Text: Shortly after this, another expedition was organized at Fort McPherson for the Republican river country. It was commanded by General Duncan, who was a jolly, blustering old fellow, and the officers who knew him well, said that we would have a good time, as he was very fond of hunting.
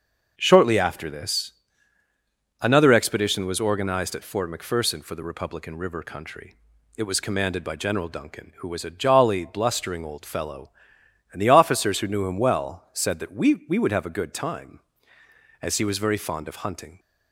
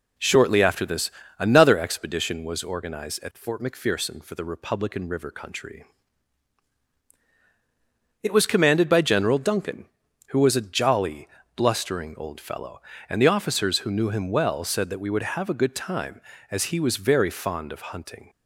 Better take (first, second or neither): second